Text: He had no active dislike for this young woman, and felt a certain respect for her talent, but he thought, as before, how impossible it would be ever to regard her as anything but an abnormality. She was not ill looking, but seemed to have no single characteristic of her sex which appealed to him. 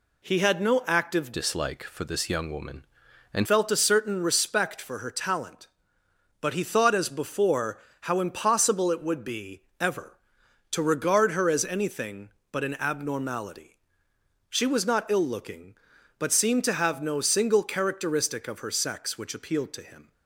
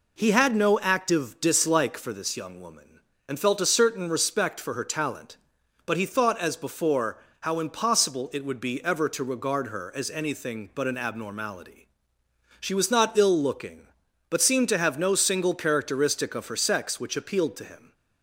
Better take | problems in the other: second | changes voice from "dislike" to "and"; from 1.3 to 3.4 s; 2.1 s long // pauses between "be" and "ever"; slight; at 9.6 s; 0.18 s long

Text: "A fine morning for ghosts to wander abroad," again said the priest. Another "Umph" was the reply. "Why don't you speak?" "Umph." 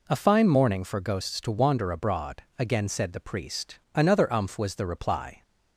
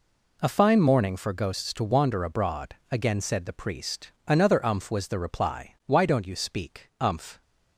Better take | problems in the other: second | stops before "Why don't you speak Umph"; at 5.4 s

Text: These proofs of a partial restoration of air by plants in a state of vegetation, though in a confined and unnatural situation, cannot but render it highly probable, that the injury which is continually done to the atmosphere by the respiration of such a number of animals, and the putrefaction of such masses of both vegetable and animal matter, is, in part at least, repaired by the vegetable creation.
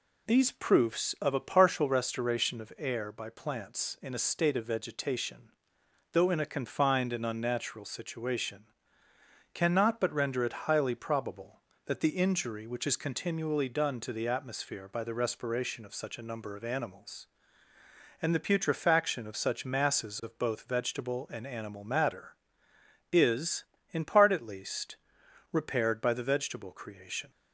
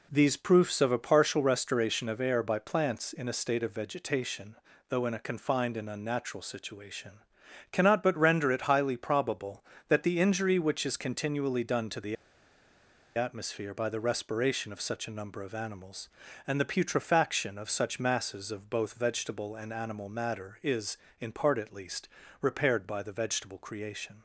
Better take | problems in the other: first | pauses between "the" and "atmosphere"; at 12.1 s; 1.0 s long

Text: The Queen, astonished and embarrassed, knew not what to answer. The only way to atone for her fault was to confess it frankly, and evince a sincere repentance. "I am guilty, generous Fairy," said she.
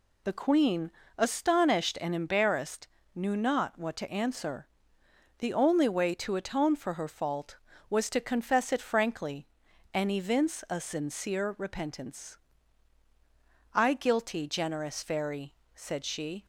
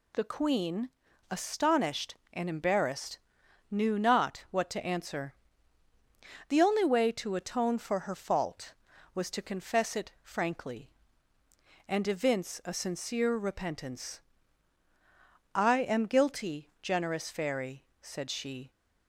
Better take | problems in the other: second | skips "am"; at 13.9 s

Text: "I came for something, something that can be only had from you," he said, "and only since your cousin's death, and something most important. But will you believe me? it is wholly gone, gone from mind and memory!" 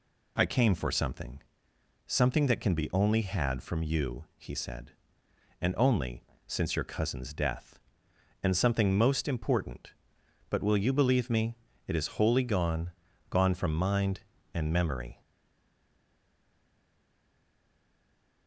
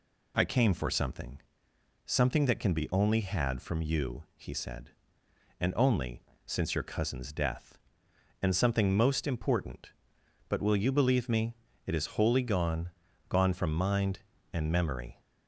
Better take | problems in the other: second | pauses between "only" and "since"; slight; at 6.2 s; 0.22 s long; slight in the second // stays silent after the last word; strong; from 15.2 s on; 3.2 s long

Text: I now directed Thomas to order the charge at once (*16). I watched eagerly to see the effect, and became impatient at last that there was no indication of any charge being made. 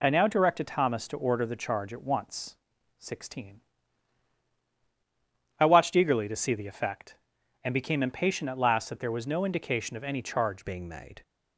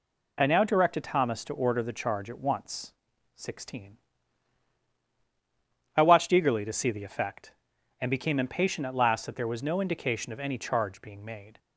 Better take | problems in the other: second | changes voice at "being"; from 10.6 s on; 0.6 s long

